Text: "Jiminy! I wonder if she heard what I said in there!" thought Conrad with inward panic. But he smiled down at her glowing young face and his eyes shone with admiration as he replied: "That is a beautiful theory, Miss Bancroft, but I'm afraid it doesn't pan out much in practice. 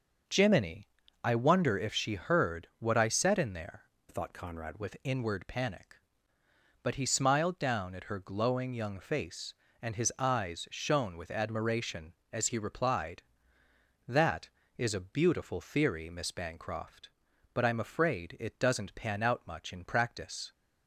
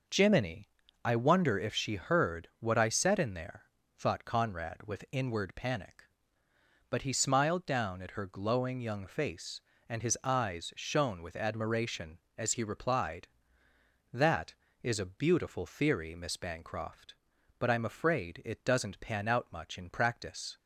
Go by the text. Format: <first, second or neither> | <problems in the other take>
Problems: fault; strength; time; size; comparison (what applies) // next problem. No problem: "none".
second | changes voice from "thought" to "Conrad"; from 4.0 to 4.7 s; 0.7 s long